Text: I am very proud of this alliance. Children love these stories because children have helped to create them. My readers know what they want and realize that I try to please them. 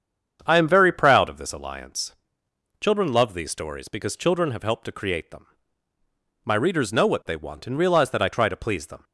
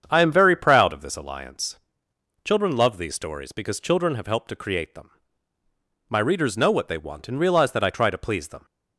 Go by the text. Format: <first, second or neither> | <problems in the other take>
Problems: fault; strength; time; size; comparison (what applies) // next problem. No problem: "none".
neither | starts louder than the rest; strong; the same in both